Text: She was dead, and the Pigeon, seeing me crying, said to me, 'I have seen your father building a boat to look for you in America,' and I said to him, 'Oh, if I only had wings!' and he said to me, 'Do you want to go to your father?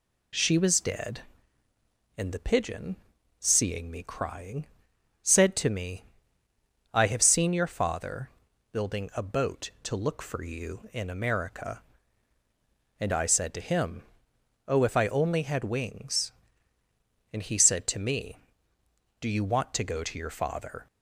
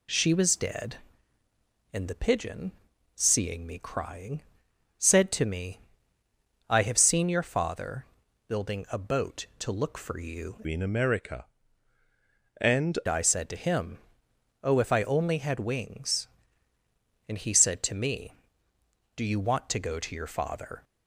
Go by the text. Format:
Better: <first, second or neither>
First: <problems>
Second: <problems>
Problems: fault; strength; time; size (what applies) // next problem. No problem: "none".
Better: first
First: pauses between "father" and "building"; at 8.2 s; 0.42 s long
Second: pauses between "father" and "building"; at 8.0 s; 0.42 s long // changes voice from "in" to "and"; from 10.6 to 12.9 s; 2.3 s long